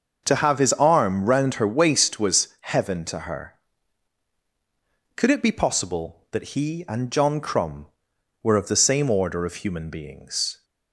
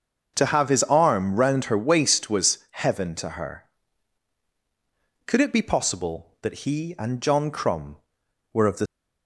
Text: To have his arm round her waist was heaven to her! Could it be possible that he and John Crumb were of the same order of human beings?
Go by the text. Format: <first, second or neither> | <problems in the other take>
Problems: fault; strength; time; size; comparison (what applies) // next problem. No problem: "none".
first | starts louder than the rest; until 1.3 s; 6 dB; also in the first // stops before "same order of human beings"; at 8.8 s